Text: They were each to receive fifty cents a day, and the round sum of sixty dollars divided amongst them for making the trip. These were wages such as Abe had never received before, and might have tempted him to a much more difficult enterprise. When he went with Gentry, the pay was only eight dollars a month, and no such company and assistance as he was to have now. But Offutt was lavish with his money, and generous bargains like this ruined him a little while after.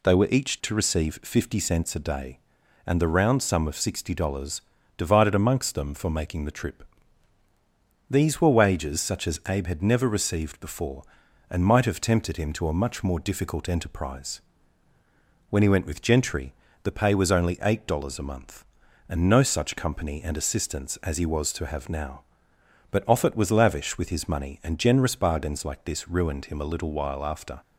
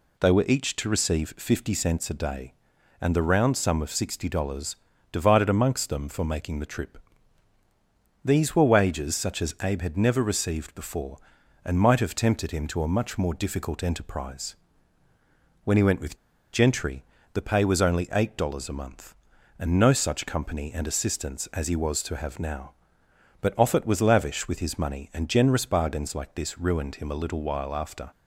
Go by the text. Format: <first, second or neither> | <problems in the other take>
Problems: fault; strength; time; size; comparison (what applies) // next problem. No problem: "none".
first | pauses between "dollars" and "divided"; slight; at 4.7 s; 0.36 s long; slight in the first // pauses between "with" and "Gentry"; slight; at 16.1 s; 0.36 s long